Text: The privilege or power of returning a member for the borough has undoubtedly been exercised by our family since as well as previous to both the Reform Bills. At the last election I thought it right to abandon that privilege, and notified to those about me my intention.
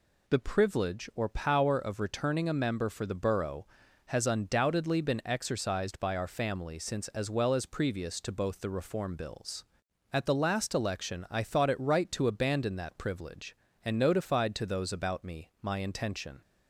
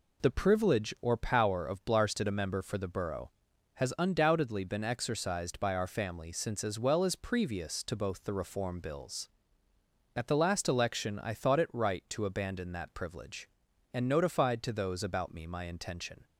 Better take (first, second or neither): first